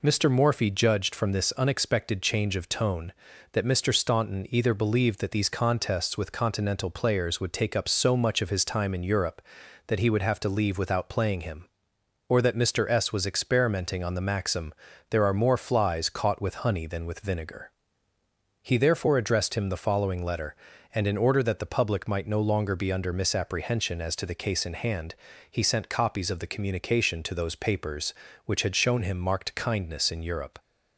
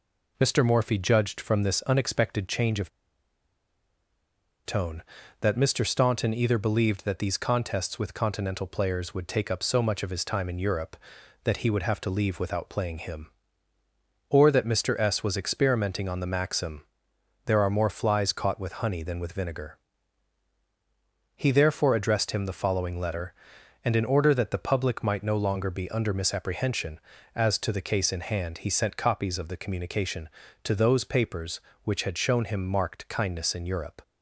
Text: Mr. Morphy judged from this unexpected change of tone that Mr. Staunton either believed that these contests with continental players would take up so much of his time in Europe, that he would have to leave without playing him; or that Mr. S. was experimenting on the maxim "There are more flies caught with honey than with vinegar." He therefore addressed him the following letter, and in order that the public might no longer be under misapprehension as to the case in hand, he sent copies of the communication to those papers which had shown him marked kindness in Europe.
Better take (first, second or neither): first